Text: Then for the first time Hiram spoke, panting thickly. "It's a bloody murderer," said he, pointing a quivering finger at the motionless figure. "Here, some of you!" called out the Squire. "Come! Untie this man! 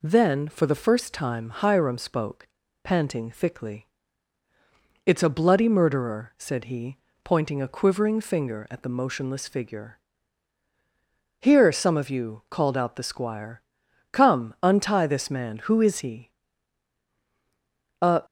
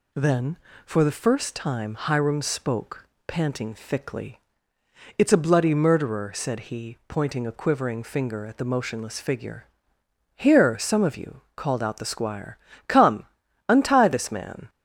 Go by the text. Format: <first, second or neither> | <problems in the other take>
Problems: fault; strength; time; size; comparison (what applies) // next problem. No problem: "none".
second | goes on to say "Who is he A"; strong; from 15.5 s on; 2.6 s long